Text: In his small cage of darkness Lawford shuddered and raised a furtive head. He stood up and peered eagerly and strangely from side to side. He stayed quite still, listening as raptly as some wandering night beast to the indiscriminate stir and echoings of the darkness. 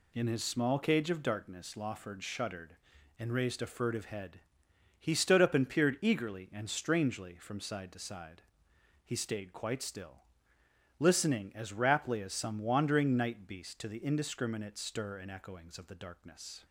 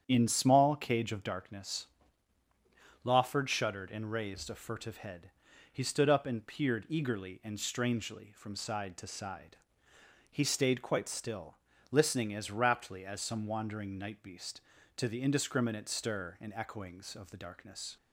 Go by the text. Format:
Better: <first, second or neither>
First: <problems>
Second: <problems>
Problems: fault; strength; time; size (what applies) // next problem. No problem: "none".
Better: first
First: none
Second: starts louder than the rest; strong; until 1.0 s; 8.5 dB // skips "his"; at 0.2 s // pauses between "darkness" and "Lawford"; at 1.8 s; 1.1 s long